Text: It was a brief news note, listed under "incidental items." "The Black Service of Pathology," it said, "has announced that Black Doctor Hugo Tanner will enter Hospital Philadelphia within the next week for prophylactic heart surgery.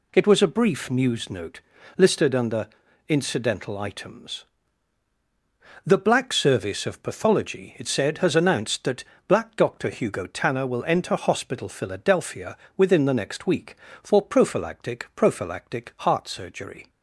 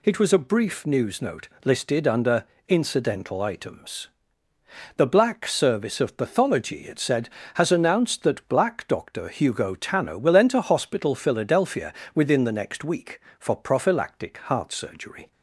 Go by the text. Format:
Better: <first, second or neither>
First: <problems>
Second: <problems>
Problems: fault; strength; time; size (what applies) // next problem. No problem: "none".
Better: second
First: pauses between "under" and "incidental"; at 2.6 s; 0.40 s long // pauses between "that" and "Black"; slight; at 9.0 s; 0.24 s long // pauses between "Philadelphia" and "within"; slight; at 12.5 s; 0.18 s long // says "prophylactic" twice; at 15.1 s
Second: pauses between "under" and "incidental"; slight; at 2.4 s; 0.24 s long // pauses between "Philadelphia" and "within"; slight; at 11.9 s; 0.22 s long